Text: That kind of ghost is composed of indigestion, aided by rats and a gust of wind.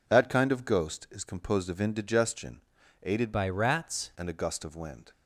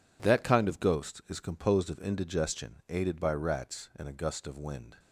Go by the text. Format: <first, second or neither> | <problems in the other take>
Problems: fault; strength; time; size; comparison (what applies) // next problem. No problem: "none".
second | changes voice from "by" to "rats"; from 3.3 to 4.1 s; 0.8 s long